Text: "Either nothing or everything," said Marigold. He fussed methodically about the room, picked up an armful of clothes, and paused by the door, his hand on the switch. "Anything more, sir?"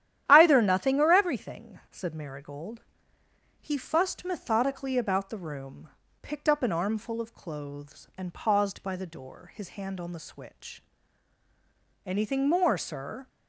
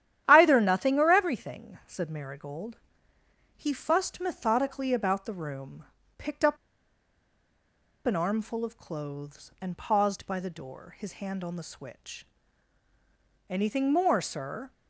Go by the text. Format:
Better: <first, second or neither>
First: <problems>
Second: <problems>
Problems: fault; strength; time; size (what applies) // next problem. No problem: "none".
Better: first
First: starts louder than the rest; strong; until 1.2 s; 11.5 dB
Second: starts louder than the rest; strong; until 1.2 s; 11.5 dB // pauses between "up" and "an"; strong; at 6.5 s; 1.4 s long